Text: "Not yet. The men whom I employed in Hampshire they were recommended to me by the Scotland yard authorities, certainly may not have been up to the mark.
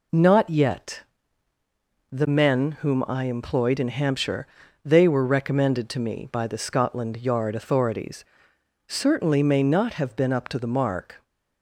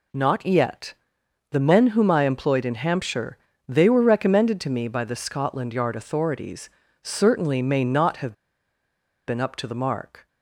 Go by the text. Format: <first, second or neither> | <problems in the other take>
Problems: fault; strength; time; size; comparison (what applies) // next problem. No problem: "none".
first | pauses between "Hampshire" and "they"; slight; at 3.3 s; 0.30 s long; also in the first // pauses between "have" and "been"; noticeable; at 8.3 s; 0.94 s long